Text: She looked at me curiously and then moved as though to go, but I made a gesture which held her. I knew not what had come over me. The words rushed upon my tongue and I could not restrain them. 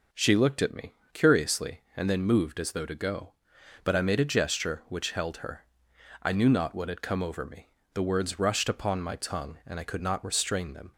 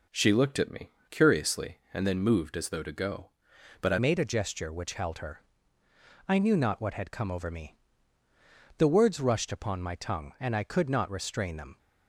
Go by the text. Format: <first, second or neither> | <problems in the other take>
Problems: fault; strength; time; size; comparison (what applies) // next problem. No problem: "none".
first | pauses between "me" and "curiously"; slight; at 0.8 s; 0.20 s long; slight in the first // changes voice at "made"; from 3.9 s on; 7.8 s long